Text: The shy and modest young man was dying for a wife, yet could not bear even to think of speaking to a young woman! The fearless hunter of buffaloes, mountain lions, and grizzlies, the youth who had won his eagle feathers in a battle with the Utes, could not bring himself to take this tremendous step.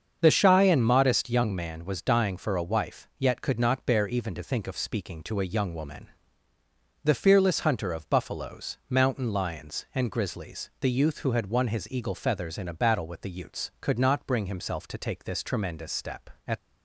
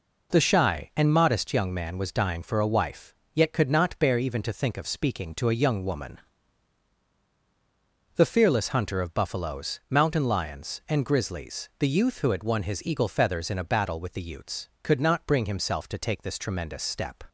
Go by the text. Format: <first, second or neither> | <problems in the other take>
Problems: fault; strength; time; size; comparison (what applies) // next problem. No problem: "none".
second | starts louder than the rest; until 1.2 s; 7 dB // goes on to say "At"; slight; from 16.4 s on; 0.06 s long